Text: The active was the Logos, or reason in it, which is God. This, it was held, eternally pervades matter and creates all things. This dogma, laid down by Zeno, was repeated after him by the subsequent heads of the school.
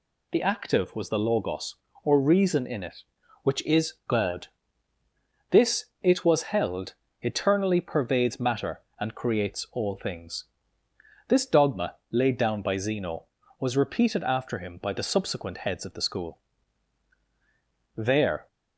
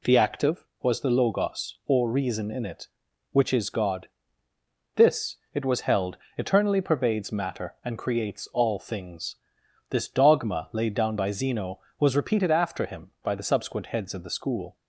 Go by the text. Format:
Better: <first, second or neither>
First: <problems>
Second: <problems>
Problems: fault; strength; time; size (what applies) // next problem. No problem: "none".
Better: second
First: goes on to say "There"; from 17.9 s on; 0.52 s long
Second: none